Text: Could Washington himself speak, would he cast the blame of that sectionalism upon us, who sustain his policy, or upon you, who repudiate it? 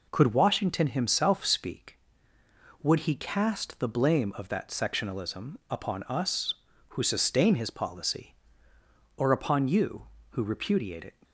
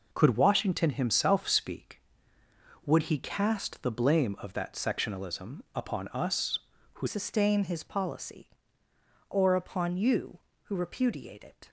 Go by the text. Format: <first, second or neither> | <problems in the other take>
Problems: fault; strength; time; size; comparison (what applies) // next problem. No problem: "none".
first | changes voice at "sustain"; from 7.0 s on; 4.6 s long